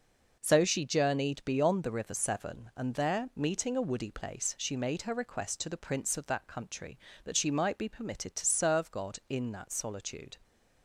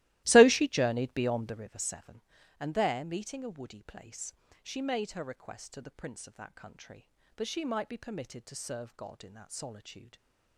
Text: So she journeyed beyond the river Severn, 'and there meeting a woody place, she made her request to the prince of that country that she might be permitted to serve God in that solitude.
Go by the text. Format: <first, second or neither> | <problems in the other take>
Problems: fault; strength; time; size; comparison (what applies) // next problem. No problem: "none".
first | starts louder than the rest; strong; until 1.8 s; 17 dB // stays silent after the last word; slight; from 10.0 s on; 0.5 s long